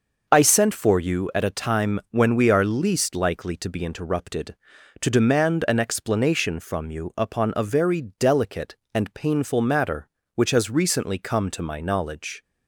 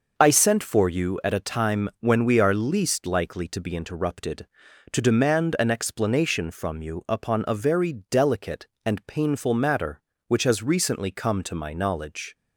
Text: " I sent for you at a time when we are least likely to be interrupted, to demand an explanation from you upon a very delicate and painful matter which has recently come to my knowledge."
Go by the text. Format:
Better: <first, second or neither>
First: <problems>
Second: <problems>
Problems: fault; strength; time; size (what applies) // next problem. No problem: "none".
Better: neither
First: starts louder than the rest; noticeable; until 1.3 s; 6 dB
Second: starts louder than the rest; noticeable; until 1.1 s; 6 dB